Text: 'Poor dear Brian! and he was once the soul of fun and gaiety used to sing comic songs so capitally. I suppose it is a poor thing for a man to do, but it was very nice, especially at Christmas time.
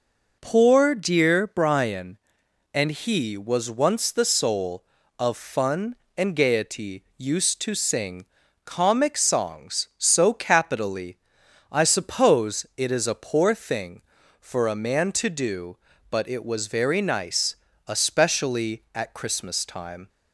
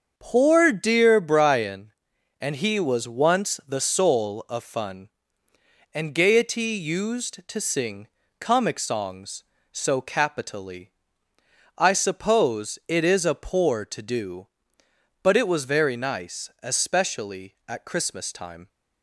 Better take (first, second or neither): first